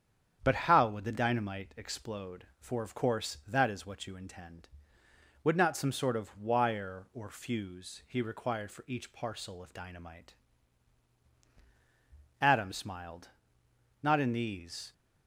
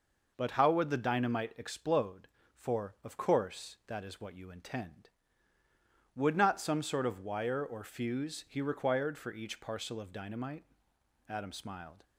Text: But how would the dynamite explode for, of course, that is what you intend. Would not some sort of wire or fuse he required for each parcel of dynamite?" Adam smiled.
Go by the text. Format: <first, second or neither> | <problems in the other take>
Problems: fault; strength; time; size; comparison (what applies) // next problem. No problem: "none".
second | starts louder than the rest; strong; until 1.4 s; 8.5 dB // goes on to say "Not in these"; noticeable; from 14.0 s on; 0.92 s long